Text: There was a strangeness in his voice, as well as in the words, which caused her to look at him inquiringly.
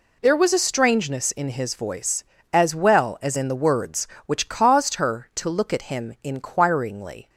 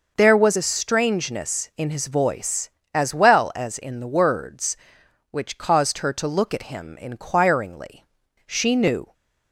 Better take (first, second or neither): first